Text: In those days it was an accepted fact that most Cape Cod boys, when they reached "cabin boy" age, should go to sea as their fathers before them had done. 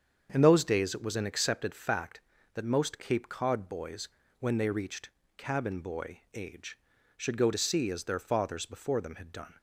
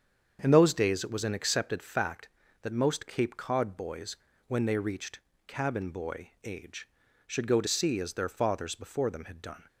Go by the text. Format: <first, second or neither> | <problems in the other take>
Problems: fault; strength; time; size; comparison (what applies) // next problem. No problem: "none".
neither | starts louder than the rest; strong; the same in both // pauses between "reached" and "cabin"; slight; the same in both